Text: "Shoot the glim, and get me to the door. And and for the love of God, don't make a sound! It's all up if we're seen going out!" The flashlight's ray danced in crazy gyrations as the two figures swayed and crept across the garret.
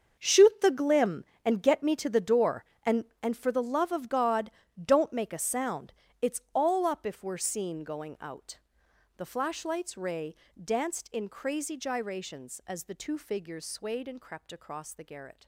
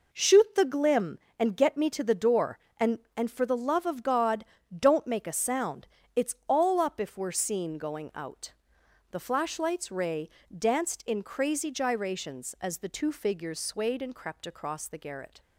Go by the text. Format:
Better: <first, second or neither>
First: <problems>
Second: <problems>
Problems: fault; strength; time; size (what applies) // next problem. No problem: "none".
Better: second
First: gets quieter; strong; throughout; 14.5 dB // pauses between "ray" and "danced"; slight; at 10.3 s; 0.30 s long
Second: pauses between "ray" and "danced"; slight; at 10.2 s; 0.30 s long